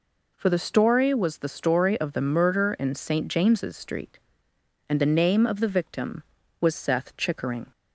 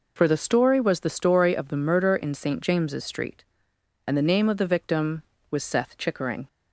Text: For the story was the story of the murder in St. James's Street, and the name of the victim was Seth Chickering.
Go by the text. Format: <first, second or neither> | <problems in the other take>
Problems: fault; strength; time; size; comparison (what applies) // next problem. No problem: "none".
neither | none